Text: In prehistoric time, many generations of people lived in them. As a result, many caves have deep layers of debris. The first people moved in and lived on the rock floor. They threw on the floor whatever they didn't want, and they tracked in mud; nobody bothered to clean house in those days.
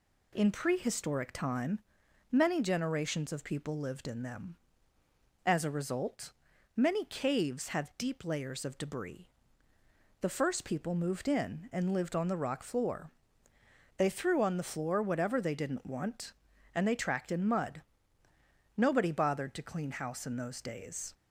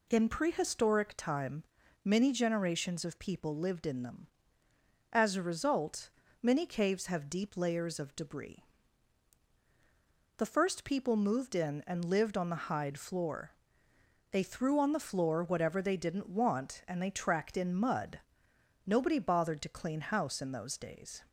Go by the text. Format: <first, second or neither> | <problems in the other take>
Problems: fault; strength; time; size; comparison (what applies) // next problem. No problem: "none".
first | says "hide" for "rock"; at 12.6 s